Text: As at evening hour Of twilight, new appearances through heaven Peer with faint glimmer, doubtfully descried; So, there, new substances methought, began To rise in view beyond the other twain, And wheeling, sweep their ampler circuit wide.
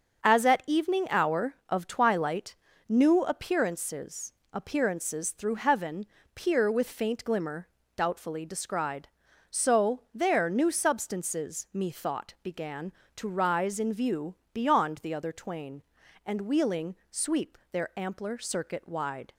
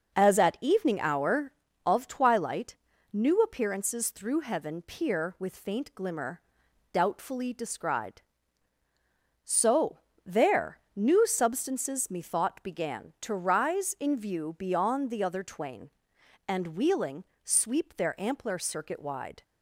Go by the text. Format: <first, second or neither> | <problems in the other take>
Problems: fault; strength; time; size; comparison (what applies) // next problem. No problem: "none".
second | starts louder than the rest; until 1.3 s; 6.5 dB; noticeable in the second // says "appearances" twice; at 4.5 s // pauses between "heaven" and "Peer"; slight; at 6.0 s; 0.28 s long // pauses between "view" and "beyond"; slight; at 14.3 s; 0.17 s long